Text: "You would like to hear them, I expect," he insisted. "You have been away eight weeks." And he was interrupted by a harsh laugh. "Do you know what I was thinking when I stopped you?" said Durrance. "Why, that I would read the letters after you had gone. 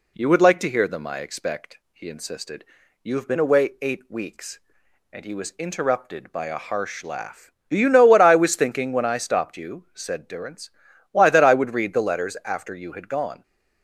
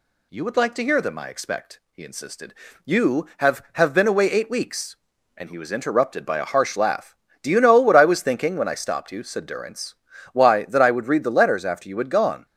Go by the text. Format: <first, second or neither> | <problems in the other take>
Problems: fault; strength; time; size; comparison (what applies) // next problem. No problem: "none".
first | says "have" twice; at 3.7 s